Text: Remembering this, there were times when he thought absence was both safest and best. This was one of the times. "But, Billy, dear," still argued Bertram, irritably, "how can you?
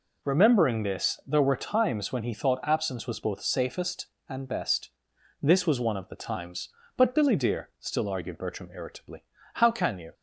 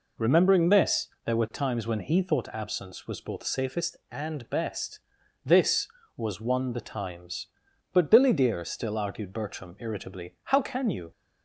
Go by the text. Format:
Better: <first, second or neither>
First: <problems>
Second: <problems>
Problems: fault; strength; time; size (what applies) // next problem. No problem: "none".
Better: first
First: none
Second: skips "of"; at 6.7 s